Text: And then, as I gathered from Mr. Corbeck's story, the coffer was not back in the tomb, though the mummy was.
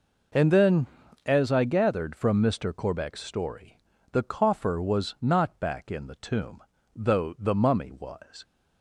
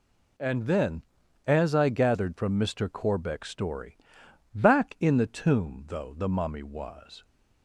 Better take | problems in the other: first | skips "the coffer was not"; at 4.2 s

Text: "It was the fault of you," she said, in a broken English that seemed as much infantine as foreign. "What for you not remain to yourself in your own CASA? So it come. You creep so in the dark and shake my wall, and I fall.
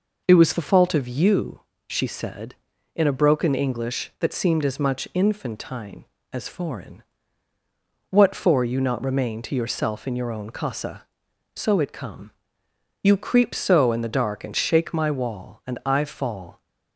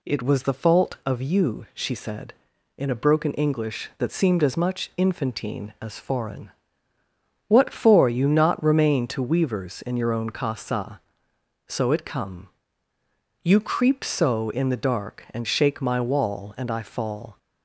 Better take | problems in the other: first | says "weavers" for "yourself"; at 9.2 s

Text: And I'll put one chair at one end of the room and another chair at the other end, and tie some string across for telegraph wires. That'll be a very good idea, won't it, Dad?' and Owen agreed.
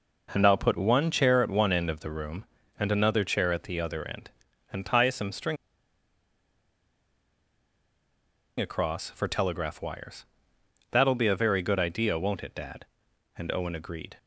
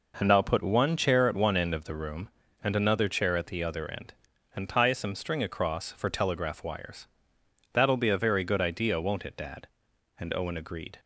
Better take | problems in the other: second | pauses between "string" and "across"; strong; at 5.5 s; 3.0 s long

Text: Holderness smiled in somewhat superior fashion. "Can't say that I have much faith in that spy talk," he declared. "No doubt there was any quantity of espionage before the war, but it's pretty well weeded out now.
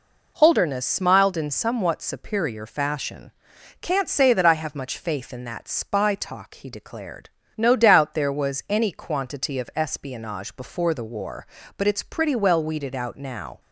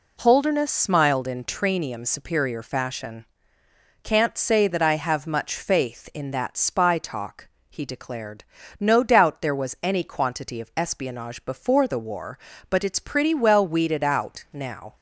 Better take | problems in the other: first | says "tranium" for "somewhat"; at 1.4 s

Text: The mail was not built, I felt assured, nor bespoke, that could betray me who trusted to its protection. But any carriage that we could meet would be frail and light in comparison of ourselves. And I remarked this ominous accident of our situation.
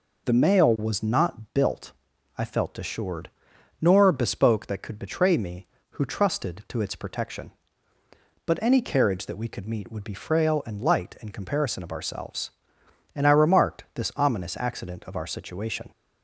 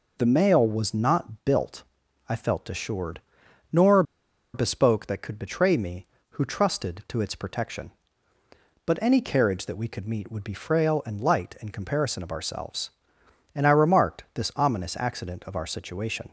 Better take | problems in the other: first | pauses between "nor" and "bespoke"; noticeable; at 4.0 s; 0.51 s long

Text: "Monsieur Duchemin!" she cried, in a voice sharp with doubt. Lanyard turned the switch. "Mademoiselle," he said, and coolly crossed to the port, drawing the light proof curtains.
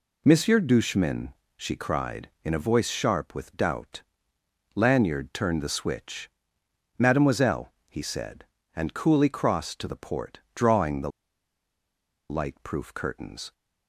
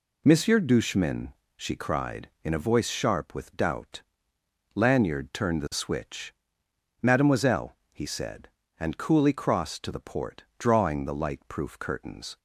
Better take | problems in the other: second | pauses between "the" and "light"; at 11.0 s; 1.1 s long

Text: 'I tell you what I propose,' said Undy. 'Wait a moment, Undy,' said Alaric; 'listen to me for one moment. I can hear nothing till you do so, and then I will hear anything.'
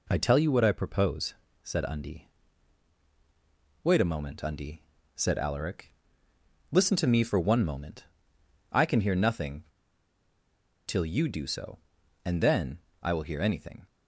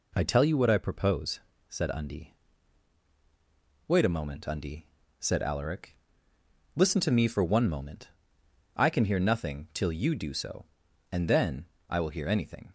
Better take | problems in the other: second | pauses between "nothing" and "till"; at 9.6 s; 1.2 s long // pauses between "then" and "I"; slight; at 12.7 s; 0.22 s long; slight in the second

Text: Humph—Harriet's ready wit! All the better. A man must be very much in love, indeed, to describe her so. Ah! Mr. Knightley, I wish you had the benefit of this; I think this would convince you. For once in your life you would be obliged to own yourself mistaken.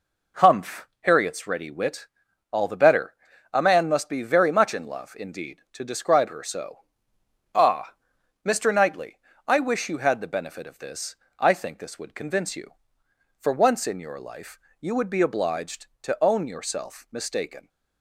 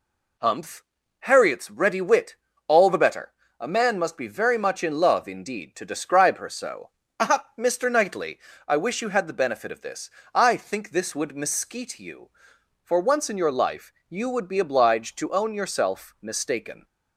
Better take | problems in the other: first | says "mesquite" for "convince"; at 11.3 s // pauses between "life" and "you"; slight; at 13.9 s; 0.18 s long; slight in the first

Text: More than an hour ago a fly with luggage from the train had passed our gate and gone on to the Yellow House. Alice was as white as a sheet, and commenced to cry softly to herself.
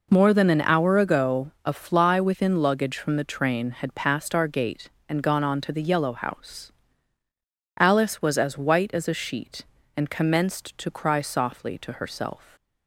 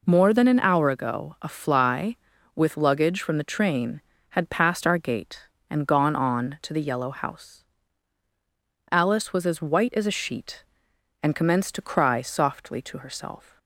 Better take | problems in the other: second | says "within" for "with"; at 2.1 s

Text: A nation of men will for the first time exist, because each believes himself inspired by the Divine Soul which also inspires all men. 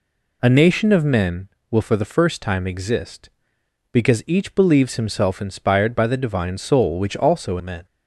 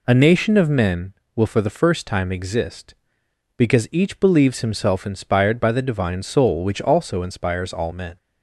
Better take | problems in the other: second | skips "inspires all"; at 7.5 s

